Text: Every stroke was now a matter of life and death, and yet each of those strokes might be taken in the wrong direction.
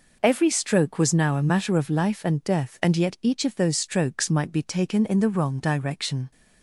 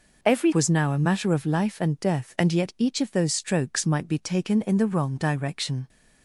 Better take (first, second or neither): first